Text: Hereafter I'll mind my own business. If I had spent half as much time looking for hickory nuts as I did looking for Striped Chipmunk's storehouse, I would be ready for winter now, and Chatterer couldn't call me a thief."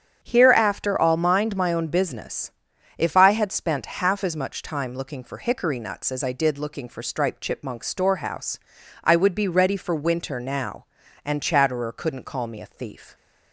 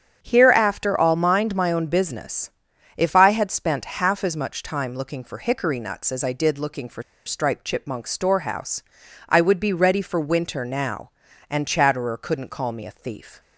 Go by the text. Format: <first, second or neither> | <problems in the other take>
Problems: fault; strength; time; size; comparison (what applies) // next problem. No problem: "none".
first | starts louder than the rest; strong; until 1.2 s; 8 dB; strong in the first // pauses between "for" and "Striped"; slight; at 7.0 s; 0.23 s long